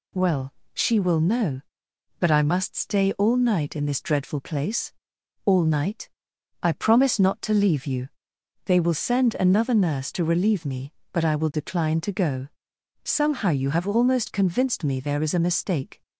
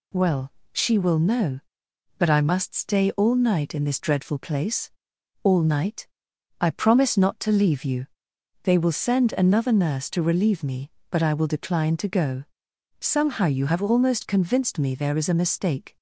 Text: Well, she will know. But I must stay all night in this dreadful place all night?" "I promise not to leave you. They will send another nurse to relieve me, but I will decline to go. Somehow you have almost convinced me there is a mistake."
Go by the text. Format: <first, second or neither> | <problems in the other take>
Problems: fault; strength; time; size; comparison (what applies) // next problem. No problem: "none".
neither | pauses between "place" and "all"; noticeable; the same in both